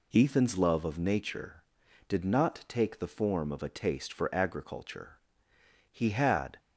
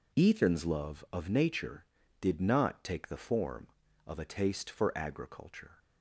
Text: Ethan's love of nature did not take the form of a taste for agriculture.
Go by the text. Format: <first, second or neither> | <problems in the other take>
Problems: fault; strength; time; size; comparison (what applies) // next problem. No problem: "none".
second | goes on to say "He had"; noticeable; from 5.8 s on; 0.70 s long